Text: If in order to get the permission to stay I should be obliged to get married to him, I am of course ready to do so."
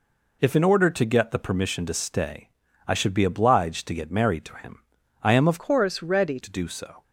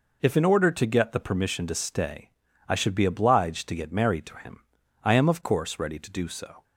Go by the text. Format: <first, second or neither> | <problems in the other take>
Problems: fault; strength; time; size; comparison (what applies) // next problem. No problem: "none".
second | pauses between "stay" and "I"; at 2.4 s; 0.38 s long; also in the second // changes voice from "course" to "ready"; from 5.5 to 6.3 s; 0.8 s long